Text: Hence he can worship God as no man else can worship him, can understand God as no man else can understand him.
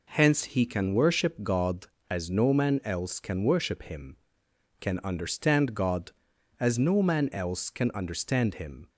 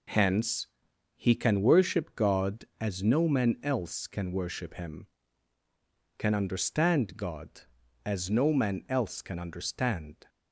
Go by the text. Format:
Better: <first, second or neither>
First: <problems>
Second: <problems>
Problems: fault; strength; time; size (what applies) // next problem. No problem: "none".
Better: first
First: none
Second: pauses between "Hence" and "he"; noticeable; at 0.6 s; 0.48 s long // stops before "him"; at 10.2 s